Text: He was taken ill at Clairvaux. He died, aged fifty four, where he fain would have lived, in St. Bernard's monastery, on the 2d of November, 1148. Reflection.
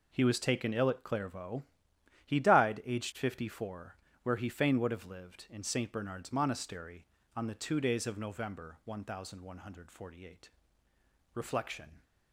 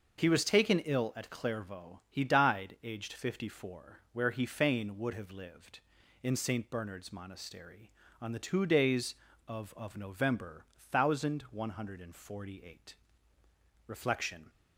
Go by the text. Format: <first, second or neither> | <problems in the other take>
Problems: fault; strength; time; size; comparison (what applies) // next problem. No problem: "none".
first | says "of" twice; at 9.7 s